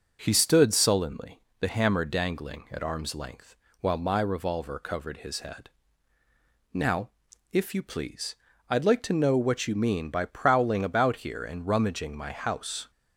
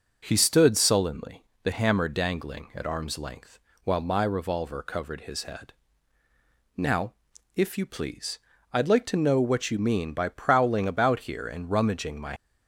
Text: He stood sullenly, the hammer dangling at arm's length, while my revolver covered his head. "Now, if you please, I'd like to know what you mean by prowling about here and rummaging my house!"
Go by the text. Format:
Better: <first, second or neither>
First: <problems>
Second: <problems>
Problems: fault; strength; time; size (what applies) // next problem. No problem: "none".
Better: first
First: none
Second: stops before "house"; at 12.3 s